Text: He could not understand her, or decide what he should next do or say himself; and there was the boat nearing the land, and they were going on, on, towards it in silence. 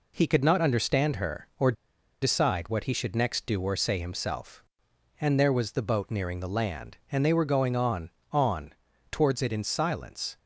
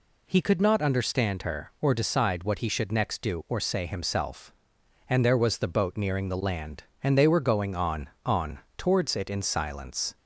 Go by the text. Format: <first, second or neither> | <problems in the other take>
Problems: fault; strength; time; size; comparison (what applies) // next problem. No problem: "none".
second | pauses between "or" and "decide"; noticeable; at 1.7 s; 0.49 s long